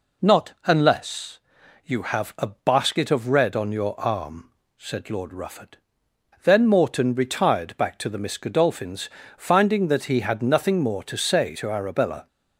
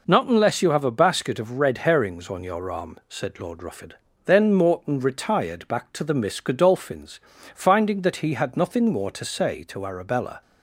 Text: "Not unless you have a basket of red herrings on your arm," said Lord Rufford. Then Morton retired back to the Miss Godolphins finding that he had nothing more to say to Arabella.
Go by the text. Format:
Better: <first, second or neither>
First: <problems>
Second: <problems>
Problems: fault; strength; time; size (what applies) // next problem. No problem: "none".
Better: second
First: pauses between "unless" and "you"; at 1.4 s; 0.44 s long // skips "herrings"; at 3.5 s // pauses between "Godolphins" and "finding"; slight; at 9.1 s; 0.26 s long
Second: pauses between "Godolphins" and "finding"; slight; at 7.2 s; 0.34 s long